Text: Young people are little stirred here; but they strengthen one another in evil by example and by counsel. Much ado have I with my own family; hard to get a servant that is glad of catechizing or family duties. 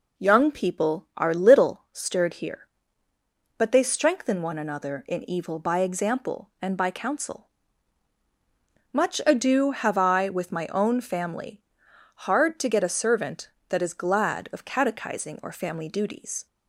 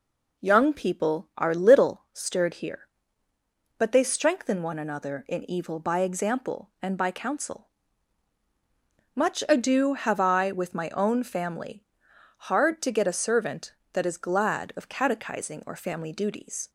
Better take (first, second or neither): neither